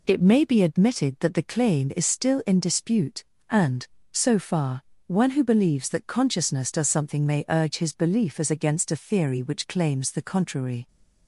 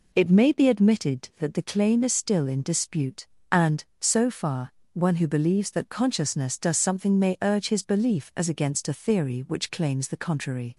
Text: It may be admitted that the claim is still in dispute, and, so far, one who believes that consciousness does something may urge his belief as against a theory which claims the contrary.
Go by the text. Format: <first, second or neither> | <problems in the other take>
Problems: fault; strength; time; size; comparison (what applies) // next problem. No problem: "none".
neither | none